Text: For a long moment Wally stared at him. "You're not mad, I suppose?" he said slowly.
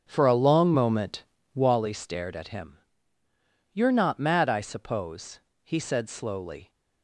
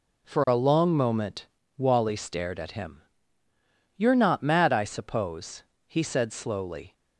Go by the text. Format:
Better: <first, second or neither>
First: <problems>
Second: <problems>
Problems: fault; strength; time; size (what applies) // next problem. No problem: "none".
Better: second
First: starts louder than the rest; strong; until 1.8 s; 8 dB // pauses between "moment" and "Wally"; slight; at 1.2 s; 0.32 s long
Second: pauses between "moment" and "Wally"; slight; at 1.4 s; 0.32 s long